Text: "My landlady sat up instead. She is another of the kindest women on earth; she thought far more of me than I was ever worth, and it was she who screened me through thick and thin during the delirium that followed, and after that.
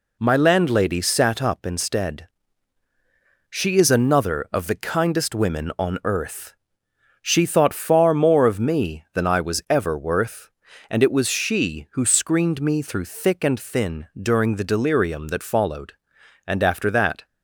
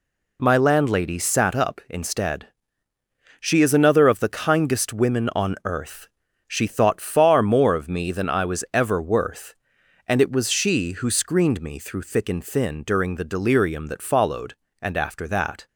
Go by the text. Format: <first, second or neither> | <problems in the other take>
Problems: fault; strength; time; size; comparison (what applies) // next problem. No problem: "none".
neither | none